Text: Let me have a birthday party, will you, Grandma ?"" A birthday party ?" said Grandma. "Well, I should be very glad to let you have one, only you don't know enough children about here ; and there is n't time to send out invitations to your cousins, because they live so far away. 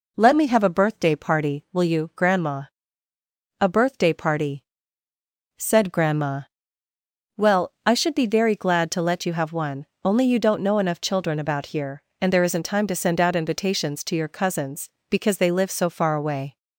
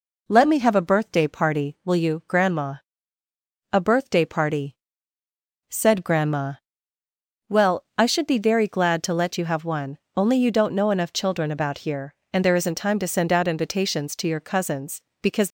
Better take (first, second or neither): first